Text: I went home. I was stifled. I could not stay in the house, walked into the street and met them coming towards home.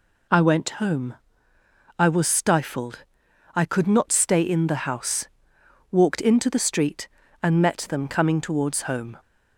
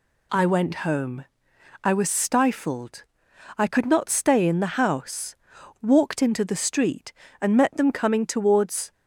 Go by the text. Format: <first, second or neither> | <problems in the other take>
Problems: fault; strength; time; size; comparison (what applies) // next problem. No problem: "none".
first | stops before "home"; at 8.9 s